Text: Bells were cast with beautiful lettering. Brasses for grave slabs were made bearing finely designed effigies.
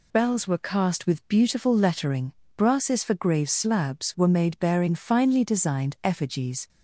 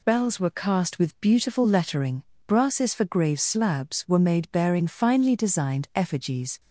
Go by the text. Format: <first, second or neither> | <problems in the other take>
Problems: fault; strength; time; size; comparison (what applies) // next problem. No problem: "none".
neither | none